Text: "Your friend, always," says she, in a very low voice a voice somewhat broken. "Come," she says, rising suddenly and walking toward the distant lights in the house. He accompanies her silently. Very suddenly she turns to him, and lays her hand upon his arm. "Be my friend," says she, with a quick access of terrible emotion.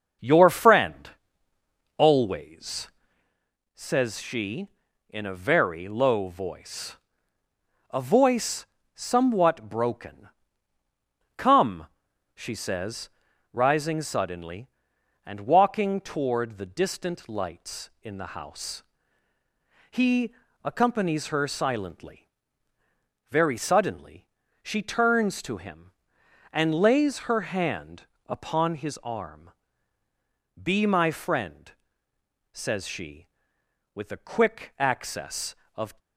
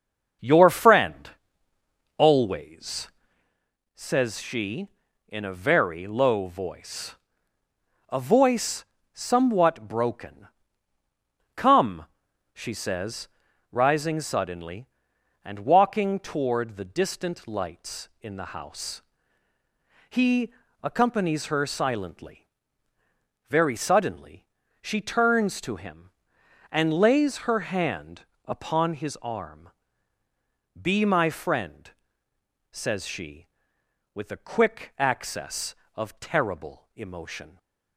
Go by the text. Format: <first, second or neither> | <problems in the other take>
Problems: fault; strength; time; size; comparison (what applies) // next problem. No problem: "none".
second | starts louder than the rest; until 2.0 s; 7 dB; also in the second // pauses between "voice" and "a"; noticeable; at 6.9 s; 0.94 s long; noticeable in the second // pauses between "voice" and "somewhat"; slight; at 8.6 s; 0.26 s long; slight in the second // pauses between "He" and "accompanies"; slight; at 20.3 s; 0.28 s long; slight in the second // pauses between "suddenly" and "she"; slight; at 24.2 s; 0.34 s long; slight in the second // pauses between "hand" and "upon"; slight; at 28.0 s; 0.22 s long; slight in the second // stops before "terrible emotion"; at 35.9 s